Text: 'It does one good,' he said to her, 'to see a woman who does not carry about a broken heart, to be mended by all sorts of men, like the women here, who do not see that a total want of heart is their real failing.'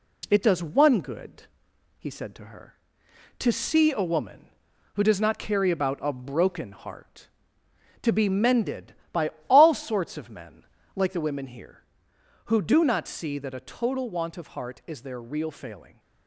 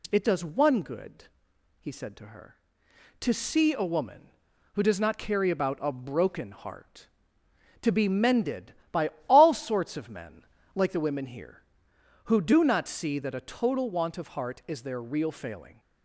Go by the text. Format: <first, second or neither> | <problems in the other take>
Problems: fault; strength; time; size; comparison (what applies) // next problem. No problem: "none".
second | gets quieter; slight; throughout; 3 dB // pauses between "by" and "all"; slight; at 9.3 s; 0.18 s long; slight in the second